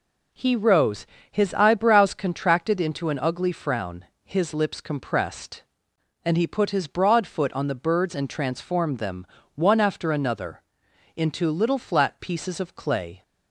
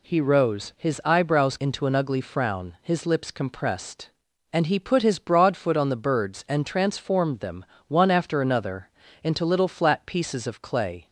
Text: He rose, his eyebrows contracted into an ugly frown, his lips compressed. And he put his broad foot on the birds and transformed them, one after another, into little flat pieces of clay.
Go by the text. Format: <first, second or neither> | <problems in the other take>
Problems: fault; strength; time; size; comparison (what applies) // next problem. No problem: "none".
first | skips "contracted"; at 1.5 s